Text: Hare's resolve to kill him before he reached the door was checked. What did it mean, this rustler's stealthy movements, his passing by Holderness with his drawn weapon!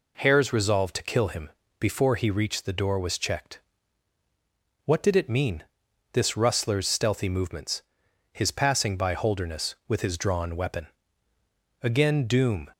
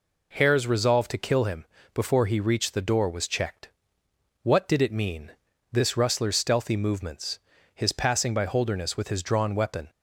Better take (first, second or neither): second